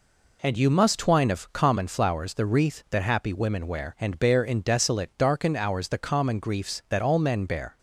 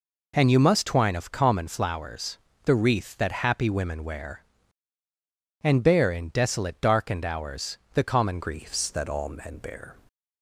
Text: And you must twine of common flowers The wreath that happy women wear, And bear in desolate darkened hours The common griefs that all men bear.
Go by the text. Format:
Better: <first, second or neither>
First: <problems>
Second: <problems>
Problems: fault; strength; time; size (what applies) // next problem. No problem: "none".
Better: first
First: none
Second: pauses between "flowers" and "The"; slight; at 2.3 s; 0.26 s long // pauses between "hours" and "The"; slight; at 7.7 s; 0.16 s long // changes voice at "griefs"; from 8.4 s on; 1.5 s long